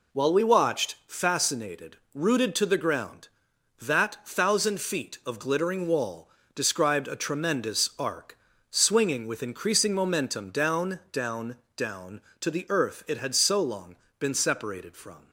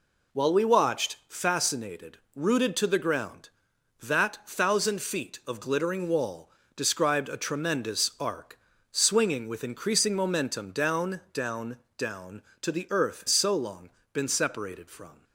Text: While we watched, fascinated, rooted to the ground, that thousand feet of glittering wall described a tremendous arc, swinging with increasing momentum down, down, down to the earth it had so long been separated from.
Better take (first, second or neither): first